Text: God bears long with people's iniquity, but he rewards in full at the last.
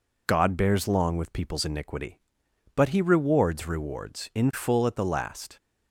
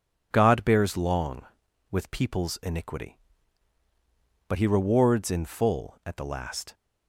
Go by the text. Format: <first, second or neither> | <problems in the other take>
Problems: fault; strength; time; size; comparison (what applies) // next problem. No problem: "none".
second | says "rewards" twice; at 3.6 s